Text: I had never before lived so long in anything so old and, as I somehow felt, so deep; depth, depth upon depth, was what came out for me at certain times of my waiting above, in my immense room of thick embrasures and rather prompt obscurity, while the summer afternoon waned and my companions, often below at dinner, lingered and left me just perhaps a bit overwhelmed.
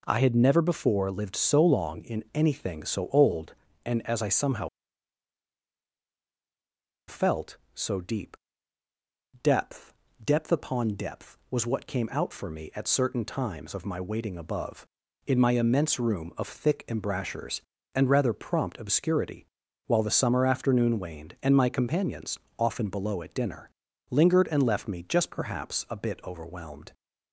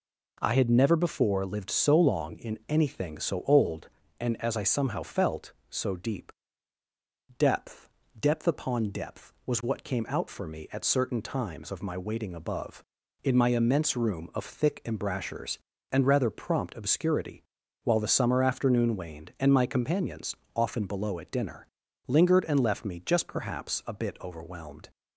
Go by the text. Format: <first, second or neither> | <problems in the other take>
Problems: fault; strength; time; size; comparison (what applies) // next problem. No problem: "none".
second | pauses between "somehow" and "felt"; strong; at 4.6 s; 2.4 s long